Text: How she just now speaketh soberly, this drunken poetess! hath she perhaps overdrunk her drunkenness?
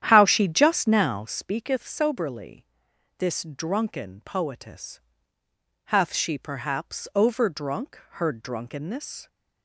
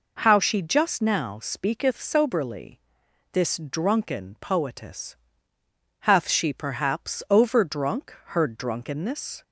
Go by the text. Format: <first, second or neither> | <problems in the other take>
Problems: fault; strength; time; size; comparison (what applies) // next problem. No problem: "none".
second | starts louder than the rest; strong; until 1.4 s; 10 dB